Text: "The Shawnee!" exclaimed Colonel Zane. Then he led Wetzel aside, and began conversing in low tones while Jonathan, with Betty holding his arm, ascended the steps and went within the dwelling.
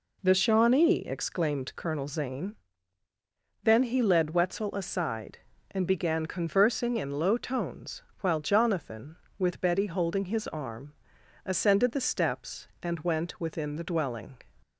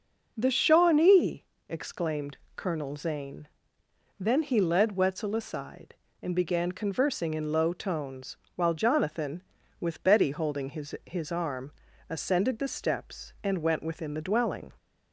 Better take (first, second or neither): first